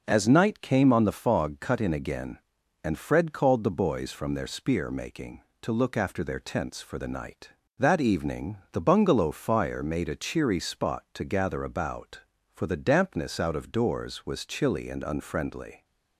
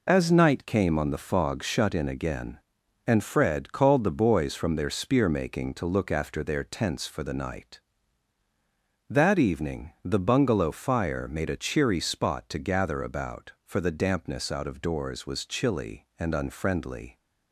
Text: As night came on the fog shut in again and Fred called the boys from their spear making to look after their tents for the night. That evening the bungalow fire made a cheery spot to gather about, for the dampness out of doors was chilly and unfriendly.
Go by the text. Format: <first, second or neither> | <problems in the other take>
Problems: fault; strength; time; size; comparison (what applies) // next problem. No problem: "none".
second | says "cut" for "shut"; at 1.6 s